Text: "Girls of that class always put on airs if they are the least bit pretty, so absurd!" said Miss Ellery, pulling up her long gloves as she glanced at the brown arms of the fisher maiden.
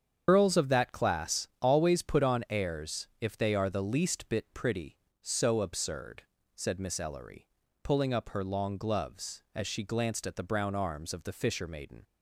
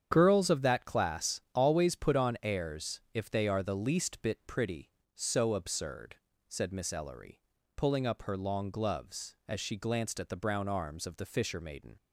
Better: second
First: loses the start of "Girls"; at 0.2 s; 100 ms // starts louder than the rest; strong; until 1.2 s; 7.5 dB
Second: starts louder than the rest; strong; until 1.1 s; 8.5 dB

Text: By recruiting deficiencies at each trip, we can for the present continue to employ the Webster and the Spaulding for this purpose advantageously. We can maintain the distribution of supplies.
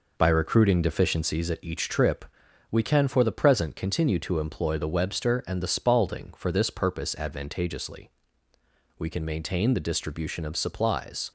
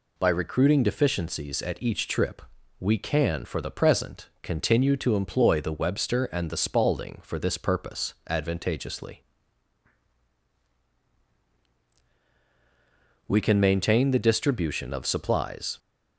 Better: second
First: starts louder than the rest; noticeable; until 1.5 s; 5 dB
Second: none

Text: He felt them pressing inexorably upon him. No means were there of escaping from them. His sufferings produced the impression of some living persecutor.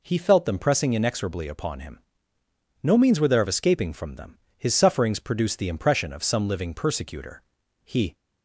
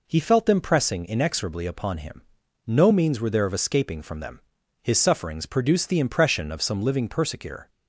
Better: second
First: goes on to say "He"; slight; from 7.8 s on; 0.30 s long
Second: none

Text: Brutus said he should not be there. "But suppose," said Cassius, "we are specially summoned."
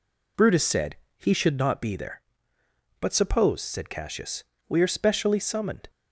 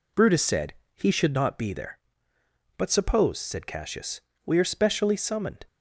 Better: neither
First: pauses between "said" and "he"; slight; at 0.9 s; 0.22 s long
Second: pauses between "said" and "he"; slight; at 0.7 s; 0.22 s long

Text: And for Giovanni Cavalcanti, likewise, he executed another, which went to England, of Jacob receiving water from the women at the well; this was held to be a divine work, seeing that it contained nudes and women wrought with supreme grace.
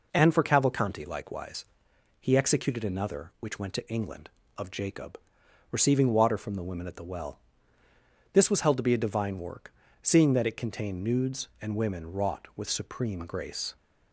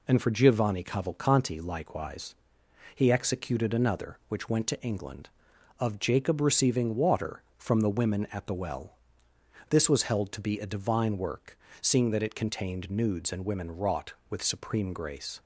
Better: second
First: skips "Giovanni"; at 0.4 s // pauses between "Jacob" and "receiving"; noticeable; at 5.1 s; 0.54 s long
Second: none

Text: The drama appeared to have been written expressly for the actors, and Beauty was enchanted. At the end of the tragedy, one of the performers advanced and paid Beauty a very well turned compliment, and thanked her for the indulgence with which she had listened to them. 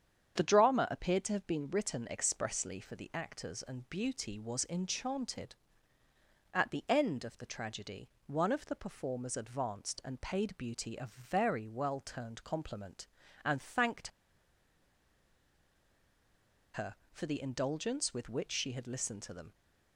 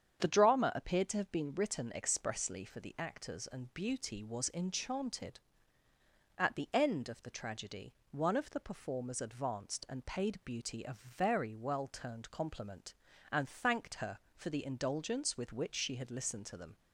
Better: second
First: starts louder than the rest; strong; until 1.4 s; 8 dB // pauses between "thanked" and "her"; strong; at 14.0 s; 2.6 s long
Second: starts louder than the rest; strong; until 1.2 s; 8 dB

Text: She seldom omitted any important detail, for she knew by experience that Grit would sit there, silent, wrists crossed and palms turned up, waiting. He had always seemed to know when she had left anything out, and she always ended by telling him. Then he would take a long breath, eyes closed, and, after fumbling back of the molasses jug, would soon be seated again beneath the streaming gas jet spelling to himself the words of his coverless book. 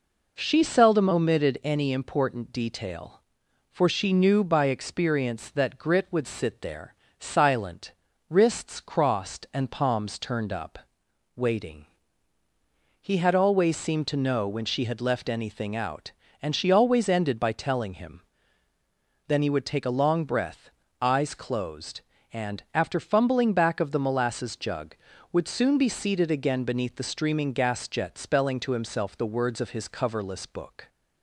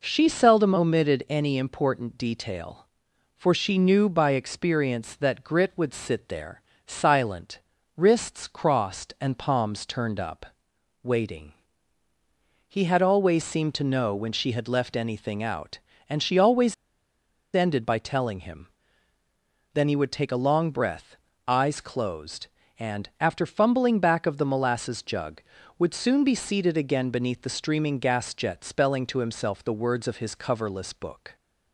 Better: first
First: none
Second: pauses between "always" and "ended"; noticeable; at 16.7 s; 0.79 s long

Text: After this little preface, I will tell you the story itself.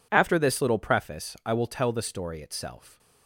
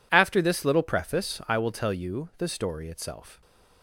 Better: second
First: skips "you"; at 1.9 s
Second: none

